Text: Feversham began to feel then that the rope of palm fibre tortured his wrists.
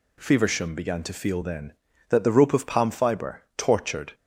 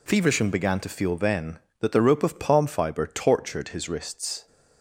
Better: second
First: pauses between "fibre" and "tortured"; slight; at 3.4 s; 0.16 s long // stops before "his wrists"; at 4.1 s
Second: none

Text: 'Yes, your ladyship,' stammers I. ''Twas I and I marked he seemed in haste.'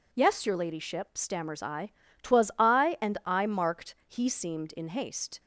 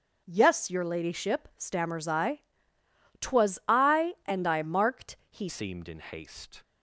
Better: first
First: none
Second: changes voice at "seemed"; from 5.4 s on; 1.2 s long

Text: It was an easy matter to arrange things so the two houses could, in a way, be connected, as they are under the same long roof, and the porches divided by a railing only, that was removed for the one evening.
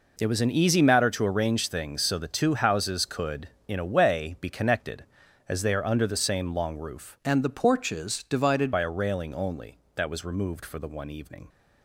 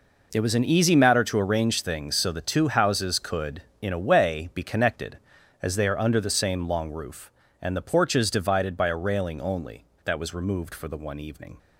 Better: second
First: changes voice from "and" to "divided"; from 7.2 to 8.7 s; 1.5 s long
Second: none

